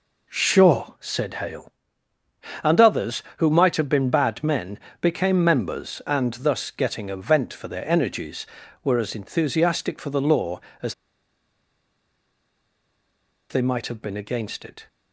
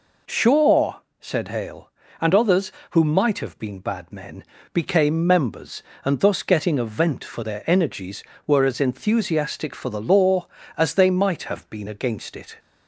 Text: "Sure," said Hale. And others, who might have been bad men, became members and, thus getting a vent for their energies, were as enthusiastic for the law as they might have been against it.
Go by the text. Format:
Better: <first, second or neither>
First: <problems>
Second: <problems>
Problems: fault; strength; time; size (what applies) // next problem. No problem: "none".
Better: second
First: pauses between "as" and "they"; strong; at 10.9 s; 2.5 s long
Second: none